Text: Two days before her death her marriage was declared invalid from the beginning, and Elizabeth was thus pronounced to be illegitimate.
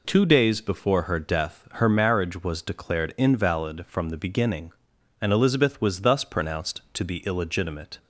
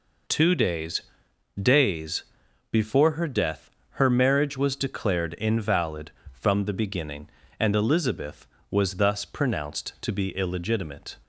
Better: first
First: none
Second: says "days" twice; at 1.6 s // pauses between "death" and "her"; slight; at 3.6 s; 0.32 s long

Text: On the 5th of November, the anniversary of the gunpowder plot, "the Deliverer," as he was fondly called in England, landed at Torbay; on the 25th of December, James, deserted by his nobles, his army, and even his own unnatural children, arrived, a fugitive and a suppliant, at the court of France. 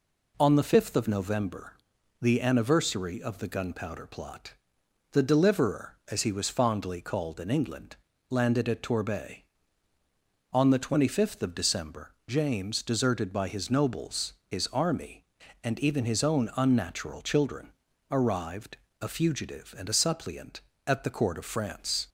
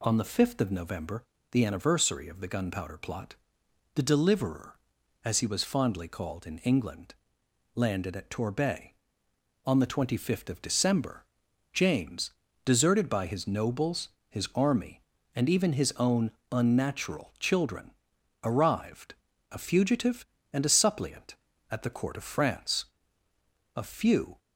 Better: first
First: none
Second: pauses between "own" and "unnatural"; slight; at 16.3 s; 0.18 s long // goes on to say "A few"; noticeable; from 23.7 s on; 0.62 s long

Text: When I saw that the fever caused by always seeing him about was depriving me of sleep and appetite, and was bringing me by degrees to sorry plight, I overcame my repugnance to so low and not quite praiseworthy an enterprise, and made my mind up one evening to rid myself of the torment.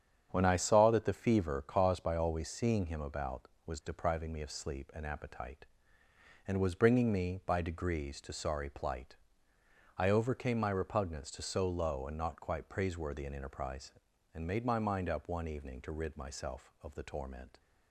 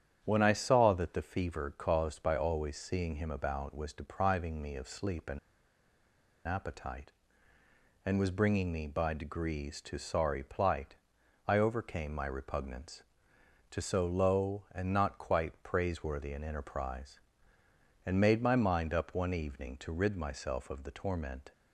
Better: first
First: starts louder than the rest; strong; until 1.3 s; 8 dB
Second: starts louder than the rest; strong; until 1.2 s; 8.5 dB // pauses between "and" and "appetite"; at 5.3 s; 1.0 s long

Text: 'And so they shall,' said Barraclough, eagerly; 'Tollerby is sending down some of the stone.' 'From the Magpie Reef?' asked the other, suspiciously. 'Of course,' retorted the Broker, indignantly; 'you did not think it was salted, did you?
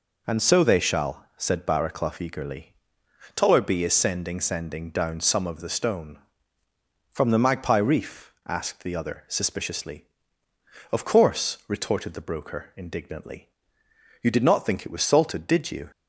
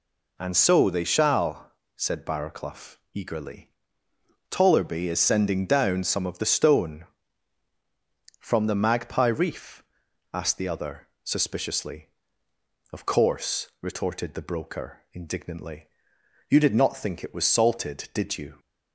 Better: second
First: says "sending" twice; at 4.4 s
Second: none

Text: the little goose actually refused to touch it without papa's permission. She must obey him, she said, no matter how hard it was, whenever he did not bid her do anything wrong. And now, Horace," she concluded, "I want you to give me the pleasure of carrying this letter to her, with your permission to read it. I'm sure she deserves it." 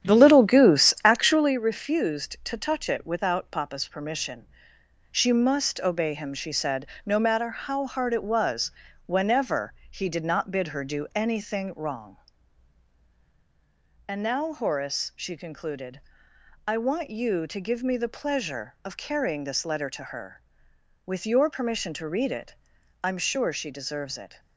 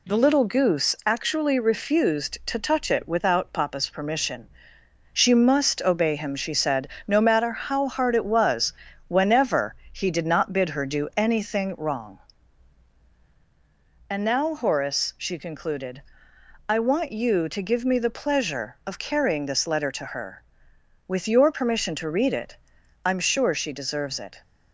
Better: second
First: starts louder than the rest; strong; until 1.5 s; 9.5 dB // pauses between "whenever" and "he"; slight; at 9.7 s; 0.16 s long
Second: pauses between "whenever" and "he"; slight; at 9.7 s; 0.16 s long

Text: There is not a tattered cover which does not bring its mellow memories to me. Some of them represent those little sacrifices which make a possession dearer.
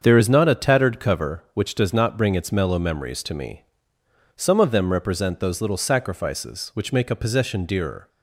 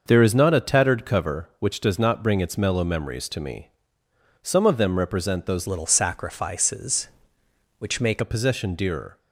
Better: first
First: starts louder than the rest; until 1.0 s; 7 dB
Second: starts louder than the rest; noticeable; until 1.0 s; 6 dB // changes voice from "little" to "make"; from 5.6 to 8.2 s; 2.6 s long

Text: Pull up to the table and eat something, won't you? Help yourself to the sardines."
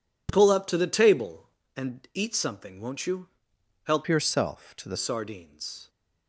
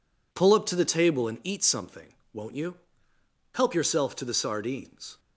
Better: second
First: changes voice from "yourself" to "the"; from 4.0 to 4.9 s; 0.9 s long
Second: none

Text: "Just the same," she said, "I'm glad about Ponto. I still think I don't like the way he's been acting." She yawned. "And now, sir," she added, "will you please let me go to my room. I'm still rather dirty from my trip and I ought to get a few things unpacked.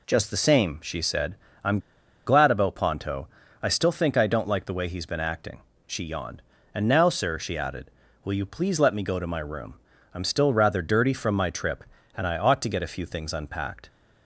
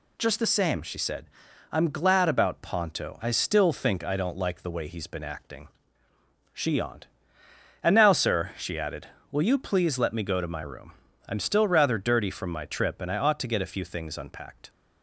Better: second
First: pauses between "I'm" and "glad"; noticeable; at 1.7 s; 0.48 s long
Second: none

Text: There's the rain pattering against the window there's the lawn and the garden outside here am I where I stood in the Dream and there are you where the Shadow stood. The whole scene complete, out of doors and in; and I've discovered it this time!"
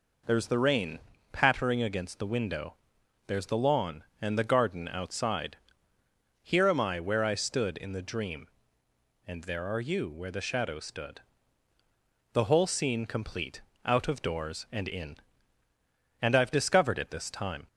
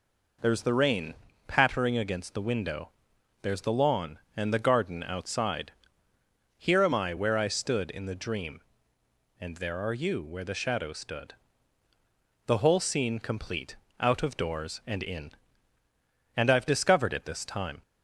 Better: neither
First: pauses between "rain" and "pattering"; slight; at 0.9 s; 0.34 s long // pauses between "window" and "there's"; noticeable; at 2.7 s; 0.52 s long // pauses between "outside" and "here"; noticeable; at 5.5 s; 0.86 s long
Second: pauses between "rain" and "pattering"; slight; at 1.1 s; 0.34 s long // pauses between "window" and "there's"; noticeable; at 2.8 s; 0.52 s long // pauses between "outside" and "here"; noticeable; at 5.7 s; 0.86 s long

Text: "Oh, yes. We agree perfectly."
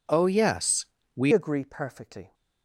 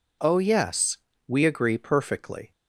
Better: second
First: changes voice at "agree"; from 1.3 s on; 1.0 s long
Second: none

